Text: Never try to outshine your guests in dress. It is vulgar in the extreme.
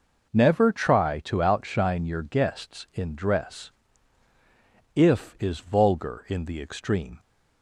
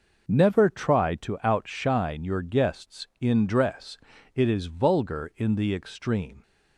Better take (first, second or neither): second